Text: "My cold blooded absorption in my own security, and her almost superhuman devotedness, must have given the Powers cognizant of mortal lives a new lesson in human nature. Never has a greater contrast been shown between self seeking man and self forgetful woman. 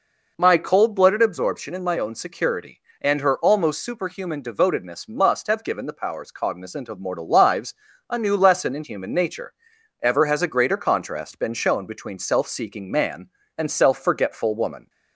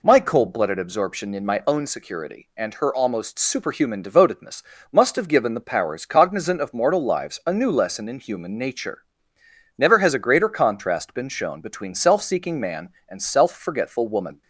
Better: second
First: pauses between "lives" and "a"; slight; at 7.7 s; 0.34 s long // says "Ever" for "Never"; at 10.0 s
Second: none

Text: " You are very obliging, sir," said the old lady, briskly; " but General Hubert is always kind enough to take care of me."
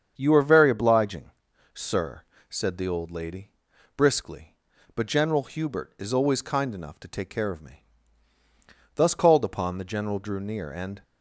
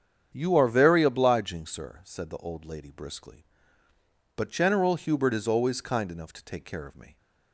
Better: second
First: starts louder than the rest; strong; until 1.1 s; 7.5 dB // goes on to say "Thus called upon the general drew near and"; strong; from 8.9 s on; 2.0 s long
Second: starts louder than the rest; strong; until 1.3 s; 8.5 dB

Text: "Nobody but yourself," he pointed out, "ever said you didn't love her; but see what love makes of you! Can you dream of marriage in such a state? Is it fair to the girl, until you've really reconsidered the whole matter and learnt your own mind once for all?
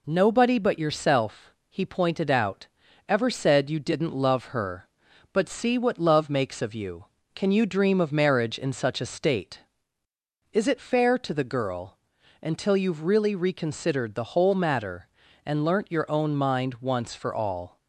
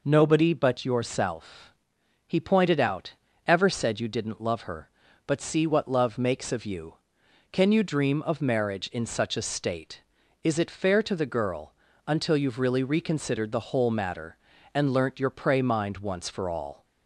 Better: first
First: none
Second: says "prey" for "own"; at 15.3 s

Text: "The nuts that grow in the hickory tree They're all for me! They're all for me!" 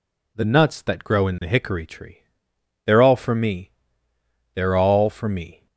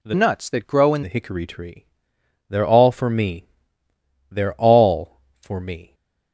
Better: first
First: pauses between "tree" and "They're"; noticeable; at 2.2 s; 0.62 s long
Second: changes voice from "nuts" to "in"; from 0.1 to 1.0 s; 0.9 s long // pauses between "tree" and "They're"; noticeable; at 1.8 s; 0.64 s long

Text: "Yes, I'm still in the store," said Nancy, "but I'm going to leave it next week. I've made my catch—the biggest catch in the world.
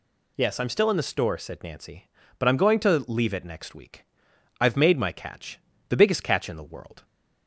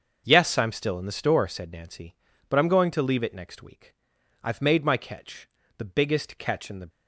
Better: first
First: none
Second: starts louder than the rest; until 1.2 s; 6.5 dB // stops before "world"; at 6.8 s

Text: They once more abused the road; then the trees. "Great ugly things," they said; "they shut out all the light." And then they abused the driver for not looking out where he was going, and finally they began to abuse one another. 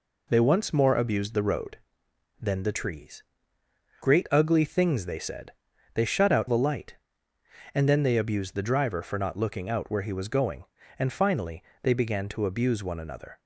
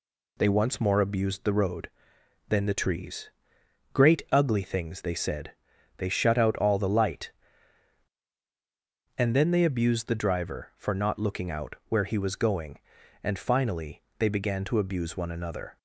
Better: second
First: skips "all"; at 6.4 s // pauses between "finally" and "they"; slight; at 11.6 s; 0.18 s long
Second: pauses between "finally" and "they"; slight; at 14.0 s; 0.16 s long

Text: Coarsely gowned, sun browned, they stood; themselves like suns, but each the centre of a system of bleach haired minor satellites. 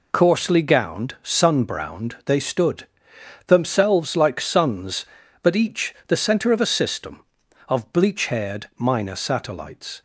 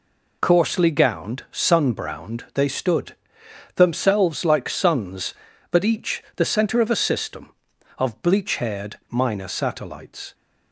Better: neither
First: none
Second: none

